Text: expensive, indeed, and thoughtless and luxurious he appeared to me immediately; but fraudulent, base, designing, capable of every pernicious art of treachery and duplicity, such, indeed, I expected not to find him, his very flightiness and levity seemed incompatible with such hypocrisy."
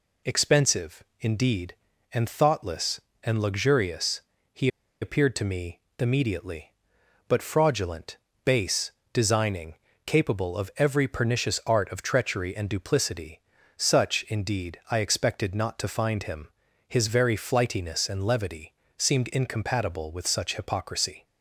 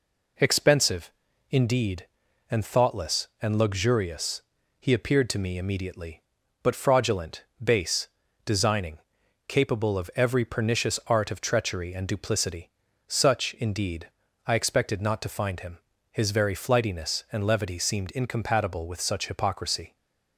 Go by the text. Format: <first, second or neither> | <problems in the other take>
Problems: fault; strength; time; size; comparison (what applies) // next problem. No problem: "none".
second | pauses between "luxurious" and "he"; slight; at 4.2 s; 0.32 s long; also in the second // pauses between "he" and "appeared"; slight; at 4.6 s; 0.34 s long // pauses between "me" and "immediately"; slight; at 5.7 s; 0.18 s long // pauses between "levity" and "seemed"; slight; at 18.7 s; 0.24 s long